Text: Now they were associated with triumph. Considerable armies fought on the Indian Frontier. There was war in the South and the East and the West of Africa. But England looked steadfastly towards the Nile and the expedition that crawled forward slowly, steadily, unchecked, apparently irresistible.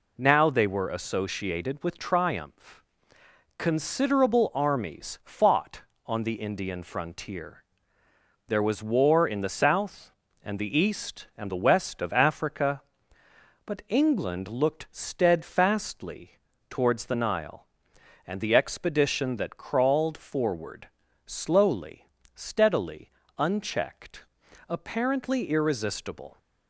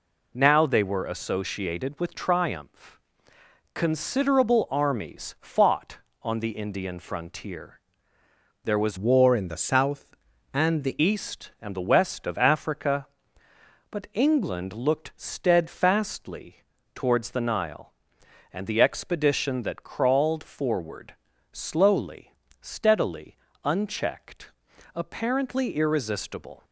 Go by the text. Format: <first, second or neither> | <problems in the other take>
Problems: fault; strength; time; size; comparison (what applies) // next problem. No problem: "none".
first | changes voice from "war" to "the"; from 8.9 to 10.9 s; 2.0 s long // pauses between "steadfastly" and "towards"; slight; at 16.6 s; 0.32 s long; slight in the first // pauses between "forward" and "slowly"; at 21.1 s; 0.38 s long; also in the first